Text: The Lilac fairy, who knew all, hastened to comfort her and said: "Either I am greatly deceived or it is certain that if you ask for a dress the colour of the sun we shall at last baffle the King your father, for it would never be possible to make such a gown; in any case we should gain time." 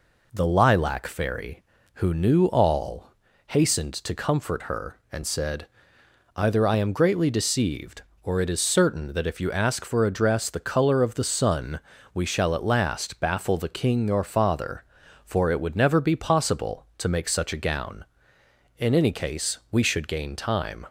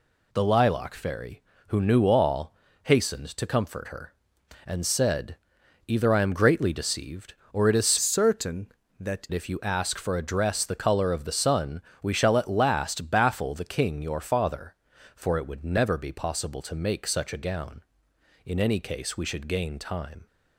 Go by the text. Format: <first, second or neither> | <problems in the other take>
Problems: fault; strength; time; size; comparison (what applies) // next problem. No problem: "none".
first | changes voice from "certain" to "that"; from 8.0 to 9.2 s; 1.2 s long // pauses between "sun" and "we"; slight; at 11.7 s; 0.22 s long; slight in the first